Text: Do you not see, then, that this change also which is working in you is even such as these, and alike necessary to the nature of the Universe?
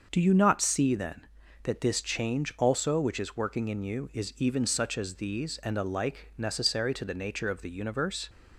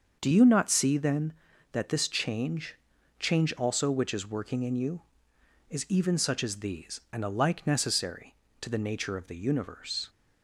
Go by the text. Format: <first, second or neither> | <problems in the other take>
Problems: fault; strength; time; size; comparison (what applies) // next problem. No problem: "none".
first | starts louder than the rest; until 1.2 s; 6.5 dB; also in the first // says "change" twice; at 3.1 s